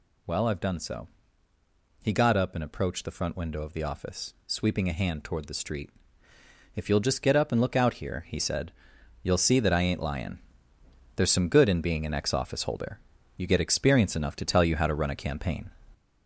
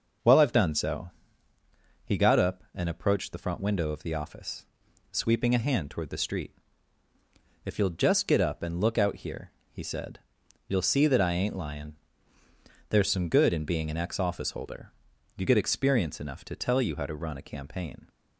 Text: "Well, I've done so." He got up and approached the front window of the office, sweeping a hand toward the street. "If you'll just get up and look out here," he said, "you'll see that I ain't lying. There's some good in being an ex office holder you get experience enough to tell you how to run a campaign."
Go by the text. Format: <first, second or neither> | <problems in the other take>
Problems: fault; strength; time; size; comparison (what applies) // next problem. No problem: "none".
second | gets louder; noticeable; throughout; 4.5 dB // pauses between "holder" and "you"; at 12.9 s; 0.38 s long; noticeable in the second